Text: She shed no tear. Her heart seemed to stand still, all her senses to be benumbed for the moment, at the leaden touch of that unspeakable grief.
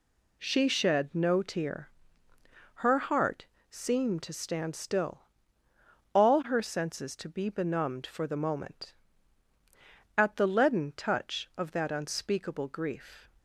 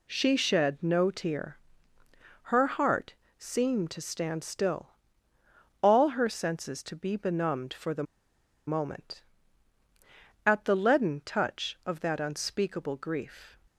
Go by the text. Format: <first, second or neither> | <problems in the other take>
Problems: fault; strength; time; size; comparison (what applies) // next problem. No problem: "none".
first | pauses between "heart" and "seemed"; slight; at 3.1 s; 0.24 s long; slight in the first // pauses between "the" and "moment"; noticeable; at 8.0 s; 0.64 s long